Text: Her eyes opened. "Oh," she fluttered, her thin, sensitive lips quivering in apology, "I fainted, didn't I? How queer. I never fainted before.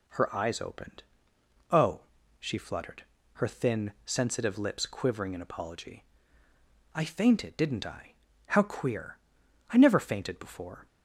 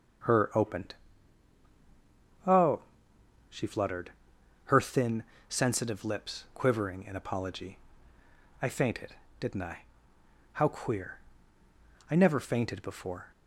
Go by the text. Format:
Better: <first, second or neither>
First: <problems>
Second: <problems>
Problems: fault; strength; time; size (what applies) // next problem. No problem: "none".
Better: first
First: none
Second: starts louder than the rest; strong; until 2.7 s; 7.5 dB // skips "eyes"; at 0.5 s